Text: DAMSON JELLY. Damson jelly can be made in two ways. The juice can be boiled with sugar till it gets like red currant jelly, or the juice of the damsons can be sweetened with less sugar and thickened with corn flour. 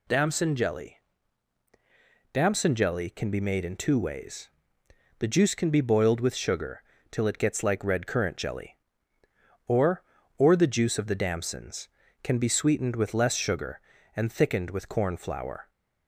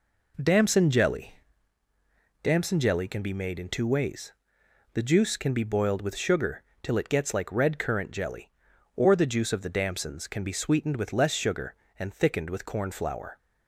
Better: second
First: pauses between "sugar" and "till"; slight; at 6.8 s; 0.30 s long // says "or" twice; at 10.3 s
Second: pauses between "sugar" and "till"; slight; at 6.6 s; 0.22 s long

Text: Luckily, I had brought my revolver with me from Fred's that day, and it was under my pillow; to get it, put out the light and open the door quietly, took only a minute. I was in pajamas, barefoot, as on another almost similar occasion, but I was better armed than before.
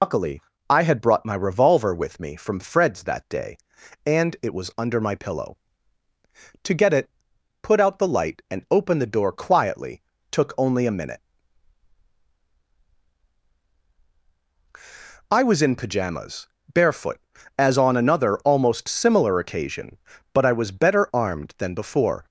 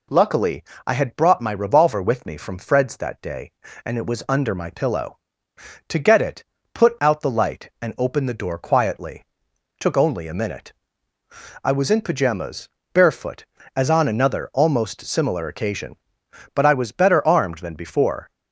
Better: second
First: loses the start of "Luckily"; at 0.0 s; 115 ms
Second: none

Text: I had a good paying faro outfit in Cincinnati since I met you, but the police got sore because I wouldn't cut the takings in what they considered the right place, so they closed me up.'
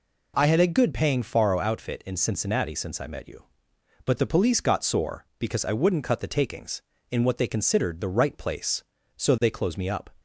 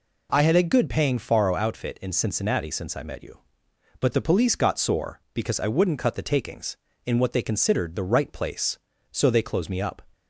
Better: neither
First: none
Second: none

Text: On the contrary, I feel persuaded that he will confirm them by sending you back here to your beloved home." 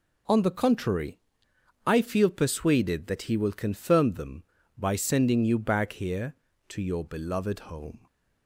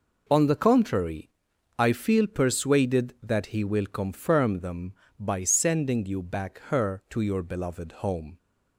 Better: first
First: none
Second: says "her" for "here"; at 6.6 s

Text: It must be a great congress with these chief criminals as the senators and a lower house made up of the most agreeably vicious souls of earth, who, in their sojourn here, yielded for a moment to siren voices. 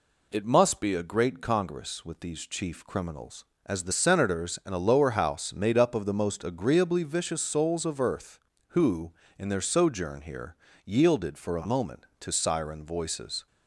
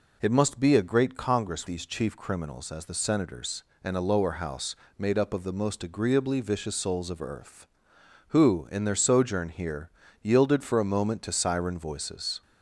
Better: first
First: none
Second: skips "with"; at 1.6 s // pauses between "house" and "made"; slight; at 4.7 s; 0.22 s long

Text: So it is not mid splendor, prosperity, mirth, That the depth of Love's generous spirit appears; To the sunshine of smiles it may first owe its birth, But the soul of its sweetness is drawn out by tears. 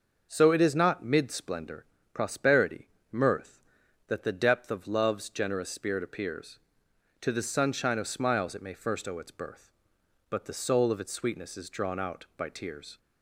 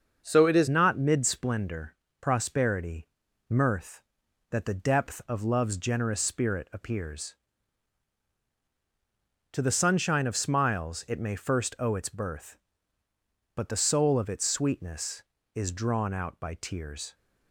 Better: first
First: starts louder than the rest; until 1.3 s; 6 dB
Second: starts louder than the rest; until 1.2 s; 6.5 dB // changes voice at "not"; from 0.6 s on; 16.5 s long

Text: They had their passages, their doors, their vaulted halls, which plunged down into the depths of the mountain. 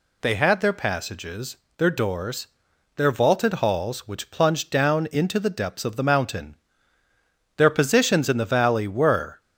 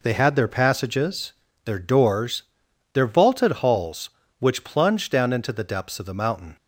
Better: second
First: goes on to say "Their positions in the valley were"; strong; from 7.5 s on; 1.8 s long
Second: none

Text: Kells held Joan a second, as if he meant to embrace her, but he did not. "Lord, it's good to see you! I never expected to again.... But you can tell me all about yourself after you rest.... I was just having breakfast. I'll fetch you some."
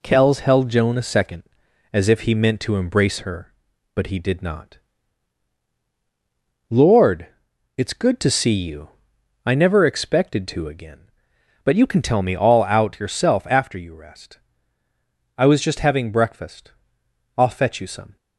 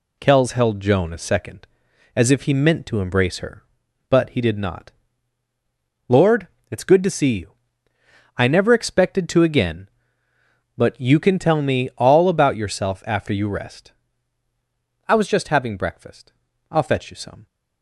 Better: second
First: says "out" for "about"; at 12.6 s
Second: none

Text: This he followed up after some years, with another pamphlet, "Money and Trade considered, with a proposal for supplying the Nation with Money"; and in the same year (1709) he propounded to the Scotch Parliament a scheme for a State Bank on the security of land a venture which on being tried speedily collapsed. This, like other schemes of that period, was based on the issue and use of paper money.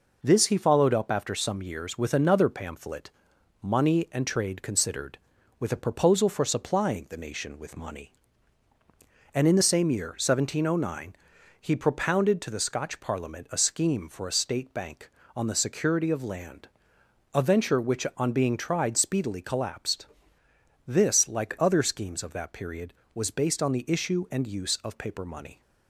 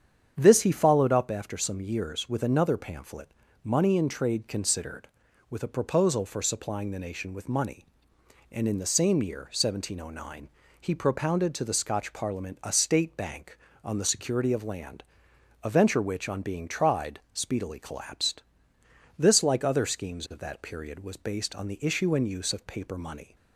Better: first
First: pauses between "land" and "a"; noticeable; at 16.6 s; 0.66 s long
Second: starts louder than the rest; strong; until 1.4 s; 8 dB // skips "a scheme for"; at 12.6 s // pauses between "land" and "a"; noticeable; at 15.0 s; 0.60 s long

